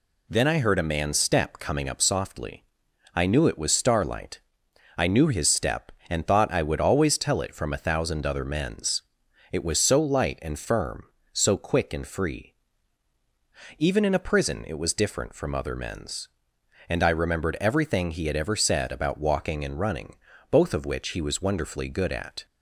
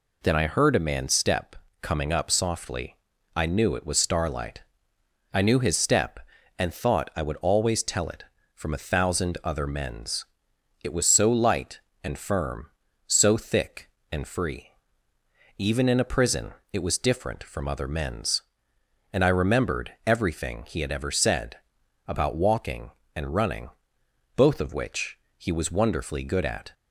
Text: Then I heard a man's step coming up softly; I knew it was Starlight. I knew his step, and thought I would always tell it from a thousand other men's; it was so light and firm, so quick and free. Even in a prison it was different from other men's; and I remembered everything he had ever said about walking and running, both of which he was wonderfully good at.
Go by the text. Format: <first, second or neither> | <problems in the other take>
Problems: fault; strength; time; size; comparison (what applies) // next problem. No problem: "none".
first | pauses between "step" and "coming"; slight; at 1.5 s; 0.26 s long // says "thick" for "quick"; at 13.3 s // pauses between "prison" and "it"; slight; at 16.5 s; 0.22 s long // pauses between "said" and "about"; noticeable; at 21.5 s; 0.54 s long // pauses between "which" and "he"; slight; at 25.1 s; 0.20 s long